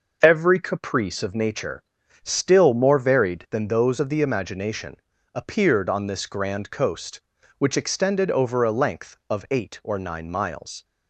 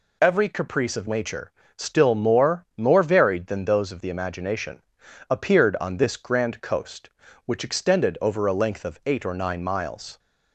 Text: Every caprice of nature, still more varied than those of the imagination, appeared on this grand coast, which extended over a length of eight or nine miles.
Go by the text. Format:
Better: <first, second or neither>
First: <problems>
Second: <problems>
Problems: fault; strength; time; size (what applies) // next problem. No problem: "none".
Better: first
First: none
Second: says "more" twice; at 2.7 s